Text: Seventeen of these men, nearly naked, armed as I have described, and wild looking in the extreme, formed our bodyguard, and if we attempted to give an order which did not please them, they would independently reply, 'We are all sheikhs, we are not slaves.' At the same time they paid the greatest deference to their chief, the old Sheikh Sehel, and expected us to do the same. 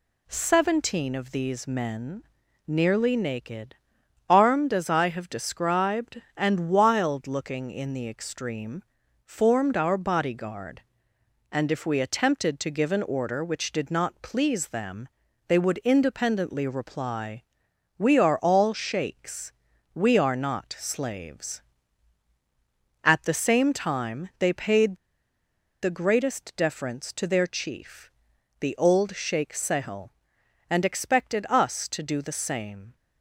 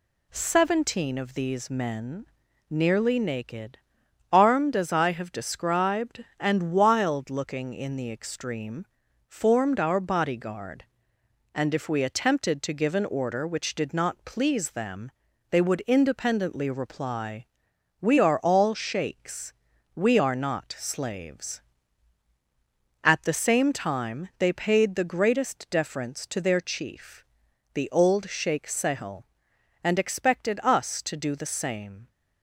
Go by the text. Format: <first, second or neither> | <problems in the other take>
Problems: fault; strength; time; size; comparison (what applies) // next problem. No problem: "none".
second | pauses between "paid" and "the"; noticeable; at 24.9 s; 0.87 s long